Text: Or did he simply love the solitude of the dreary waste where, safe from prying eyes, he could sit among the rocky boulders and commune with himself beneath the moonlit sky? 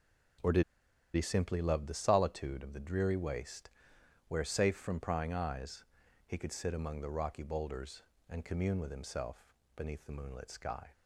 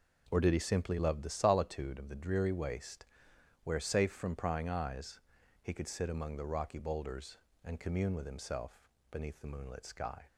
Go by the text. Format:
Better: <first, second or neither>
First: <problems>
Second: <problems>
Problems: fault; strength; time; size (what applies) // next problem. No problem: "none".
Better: second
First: pauses between "did" and "he"; noticeable; at 0.6 s; 0.52 s long // pauses between "waste" and "where"; noticeable; at 3.6 s; 0.58 s long // pauses between "himself" and "beneath"; slight; at 9.4 s; 0.32 s long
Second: pauses between "waste" and "where"; noticeable; at 3.0 s; 0.58 s long // pauses between "himself" and "beneath"; slight; at 8.7 s; 0.32 s long